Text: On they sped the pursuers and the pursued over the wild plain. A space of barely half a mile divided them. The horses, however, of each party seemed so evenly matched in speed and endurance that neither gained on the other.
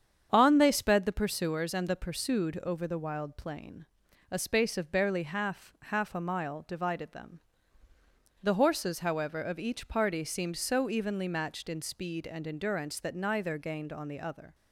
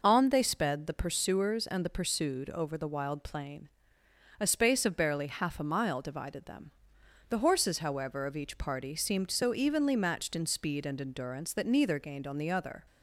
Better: second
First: starts louder than the rest; strong; until 1.3 s; 8 dB // says "half" twice; at 5.8 s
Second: none

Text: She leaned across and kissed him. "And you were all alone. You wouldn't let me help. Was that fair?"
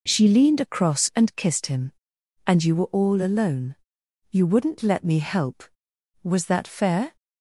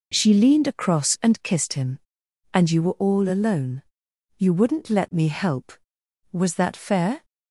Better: neither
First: none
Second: none

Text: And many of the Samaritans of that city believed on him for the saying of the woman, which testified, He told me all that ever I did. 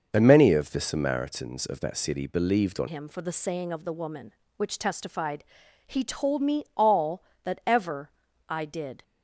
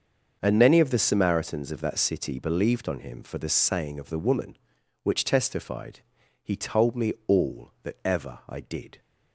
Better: second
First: starts louder than the rest; noticeable; until 1.1 s; 6 dB // changes voice at "him"; from 2.8 s on; 6.2 s long // pauses between "ever" and "I"; at 8.1 s; 0.38 s long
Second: starts louder than the rest; until 1.4 s; 6.5 dB

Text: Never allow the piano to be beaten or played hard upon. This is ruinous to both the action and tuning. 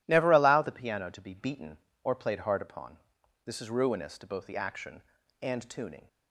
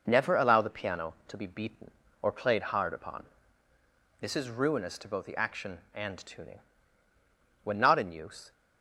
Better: first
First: none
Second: goes on to say "When not in use"; noticeable; from 7.6 s on; 0.88 s long

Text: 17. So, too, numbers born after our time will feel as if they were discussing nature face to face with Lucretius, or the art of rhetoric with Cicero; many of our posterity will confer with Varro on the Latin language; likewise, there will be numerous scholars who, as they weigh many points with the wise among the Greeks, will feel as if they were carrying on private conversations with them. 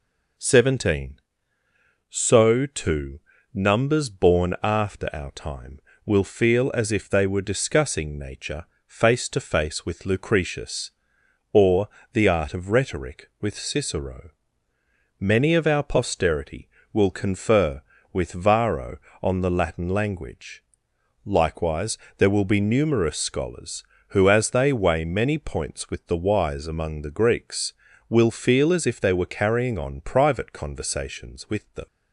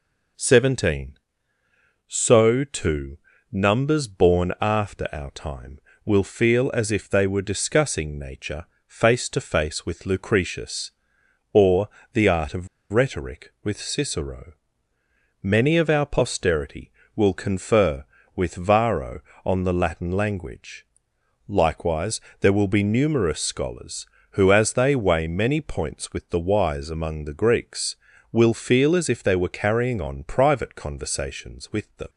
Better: first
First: pauses between "nature" and "face"; slight; at 8.6 s; 0.20 s long // pauses between "or" and "the"; slight; at 11.8 s; 0.28 s long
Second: pauses between "nature" and "face"; slight; at 8.6 s; 0.20 s long // pauses between "or" and "the"; slight; at 11.8 s; 0.28 s long // pauses between "of" and "rhetoric"; slight; at 12.6 s; 0.25 s long

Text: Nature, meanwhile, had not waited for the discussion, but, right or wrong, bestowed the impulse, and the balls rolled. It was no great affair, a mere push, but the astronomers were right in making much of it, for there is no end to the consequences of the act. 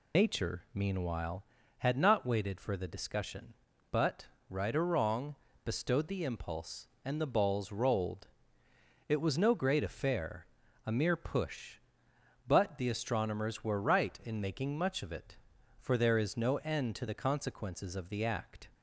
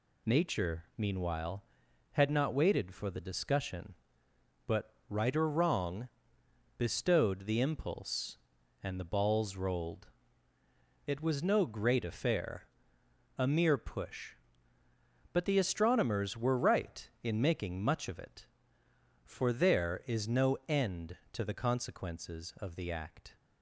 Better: second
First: loses the start of "Nature"; at 0.1 s; 110 ms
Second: none

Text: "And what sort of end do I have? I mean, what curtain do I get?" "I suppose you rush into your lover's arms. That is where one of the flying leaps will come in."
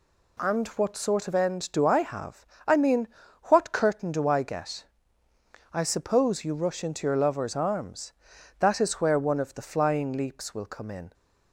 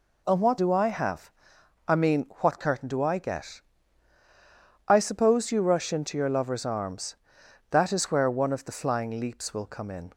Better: first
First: none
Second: skips "sort of end"; at 0.5 s

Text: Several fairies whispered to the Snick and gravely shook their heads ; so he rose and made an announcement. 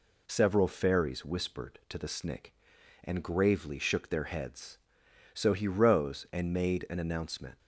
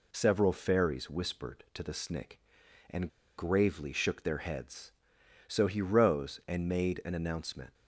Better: first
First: none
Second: pauses between "and" and "gravely"; slight; at 3.0 s; 0.27 s long

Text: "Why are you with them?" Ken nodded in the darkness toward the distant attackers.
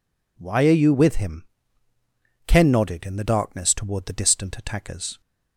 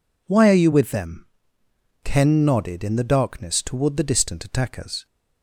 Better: second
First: says "him" for "them"; at 1.1 s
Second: none

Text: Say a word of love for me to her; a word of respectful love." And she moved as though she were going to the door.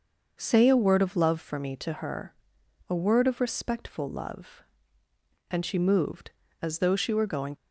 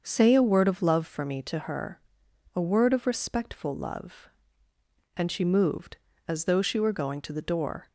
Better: second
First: starts louder than the rest; noticeable; until 1.3 s; 6 dB // stops before "to the door"; at 7.5 s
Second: starts louder than the rest; until 1.0 s; 6.5 dB

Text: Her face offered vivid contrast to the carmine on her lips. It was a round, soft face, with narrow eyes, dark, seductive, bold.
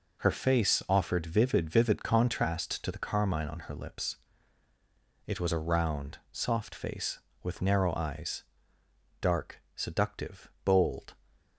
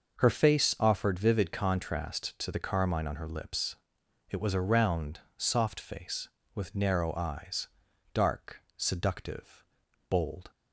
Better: second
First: says "vivid" twice; at 1.6 s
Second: none

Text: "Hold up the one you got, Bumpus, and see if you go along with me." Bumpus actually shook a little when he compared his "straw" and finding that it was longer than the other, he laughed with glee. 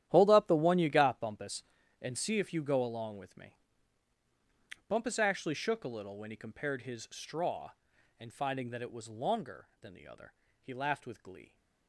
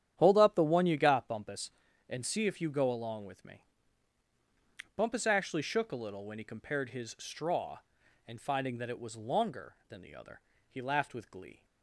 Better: second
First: gets quieter; strong; throughout; 14 dB // starts louder than the rest; strong; until 1.0 s; 11.5 dB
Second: starts louder than the rest; strong; until 1.1 s; 10 dB

